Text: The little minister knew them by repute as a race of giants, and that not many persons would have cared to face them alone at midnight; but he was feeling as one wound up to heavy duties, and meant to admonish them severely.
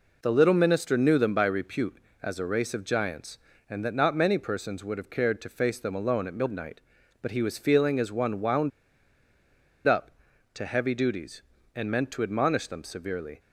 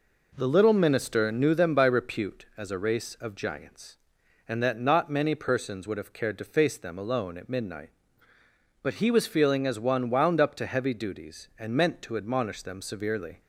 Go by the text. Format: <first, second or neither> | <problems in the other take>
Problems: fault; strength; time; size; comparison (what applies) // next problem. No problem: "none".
second | pauses between "wound" and "up"; at 8.7 s; 1.1 s long